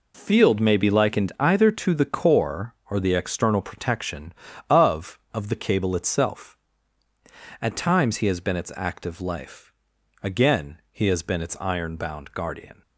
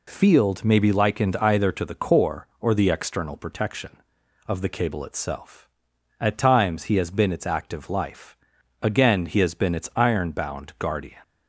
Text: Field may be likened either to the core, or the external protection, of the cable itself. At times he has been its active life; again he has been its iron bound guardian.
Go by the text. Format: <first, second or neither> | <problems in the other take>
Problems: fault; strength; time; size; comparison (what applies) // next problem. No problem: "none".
second | says "of" twice; at 5.3 s